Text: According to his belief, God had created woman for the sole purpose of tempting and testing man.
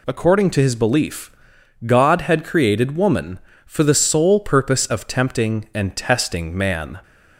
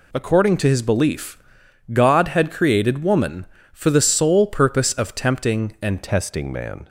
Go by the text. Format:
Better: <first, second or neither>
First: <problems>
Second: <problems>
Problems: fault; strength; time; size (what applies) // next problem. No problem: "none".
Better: first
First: none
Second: changes voice at "testing"; from 6.0 s on; 0.8 s long